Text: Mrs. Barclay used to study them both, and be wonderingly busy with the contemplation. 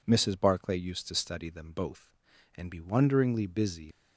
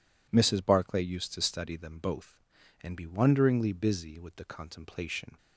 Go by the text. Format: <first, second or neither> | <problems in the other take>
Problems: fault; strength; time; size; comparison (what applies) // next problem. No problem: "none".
second | stops before "with the contemplation"; at 3.9 s